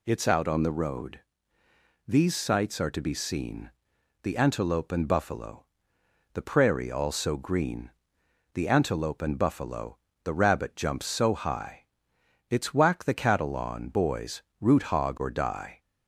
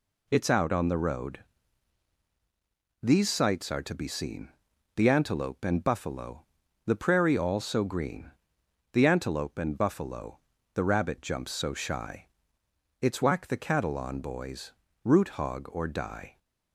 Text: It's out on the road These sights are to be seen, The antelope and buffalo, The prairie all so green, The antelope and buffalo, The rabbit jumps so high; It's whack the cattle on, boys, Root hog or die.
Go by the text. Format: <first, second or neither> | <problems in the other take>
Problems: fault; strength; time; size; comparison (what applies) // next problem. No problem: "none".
first | pauses between "road" and "These"; strong; at 1.3 s; 1.6 s long; noticeable in the first // says "shy" for "high"; at 11.7 s